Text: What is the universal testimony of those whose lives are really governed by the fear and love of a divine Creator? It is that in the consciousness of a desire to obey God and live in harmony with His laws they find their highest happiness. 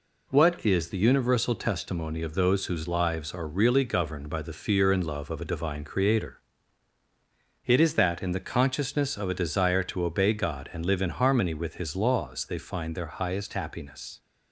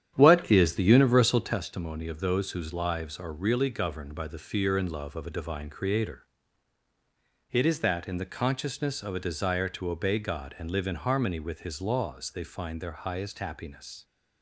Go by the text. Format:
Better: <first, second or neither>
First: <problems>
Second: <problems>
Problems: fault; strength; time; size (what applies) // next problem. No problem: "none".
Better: first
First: none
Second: starts louder than the rest; strong; until 1.6 s; 10 dB